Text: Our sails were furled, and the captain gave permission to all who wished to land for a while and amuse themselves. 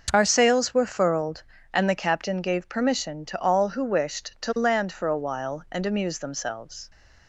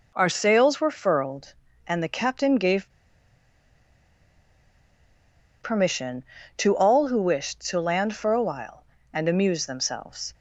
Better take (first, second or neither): first